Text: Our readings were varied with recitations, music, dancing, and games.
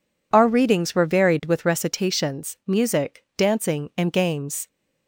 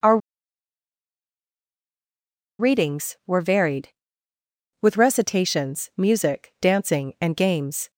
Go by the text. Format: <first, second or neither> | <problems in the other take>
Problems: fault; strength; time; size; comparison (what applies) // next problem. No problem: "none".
first | pauses between "Our" and "readings"; strong; at 0.1 s; 2.4 s long